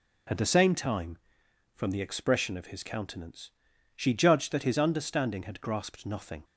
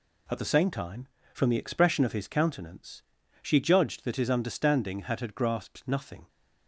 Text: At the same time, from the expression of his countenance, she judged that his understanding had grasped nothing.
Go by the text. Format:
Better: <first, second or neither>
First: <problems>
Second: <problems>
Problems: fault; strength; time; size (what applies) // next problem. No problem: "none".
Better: first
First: none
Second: says "had" twice; at 5.2 s